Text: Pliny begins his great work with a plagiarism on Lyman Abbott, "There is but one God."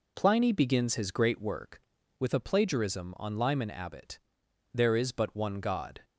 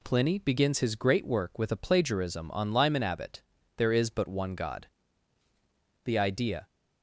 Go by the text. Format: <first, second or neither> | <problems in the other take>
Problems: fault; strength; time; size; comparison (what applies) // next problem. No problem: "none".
first | goes on to say "The idea"; from 6.0 s on; 0.60 s long